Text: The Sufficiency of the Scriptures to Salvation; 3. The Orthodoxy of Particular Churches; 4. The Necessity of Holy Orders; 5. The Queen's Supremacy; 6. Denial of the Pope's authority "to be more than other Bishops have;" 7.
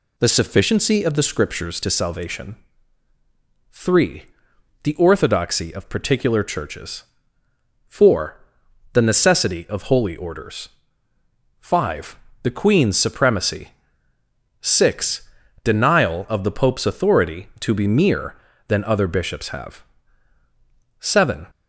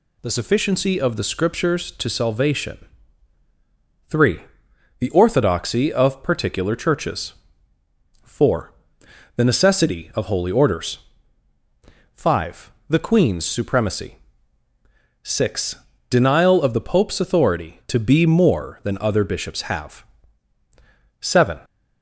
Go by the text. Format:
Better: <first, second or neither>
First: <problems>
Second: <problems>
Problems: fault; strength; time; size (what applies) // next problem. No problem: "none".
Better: second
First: says "mere" for "more"; at 17.8 s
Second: none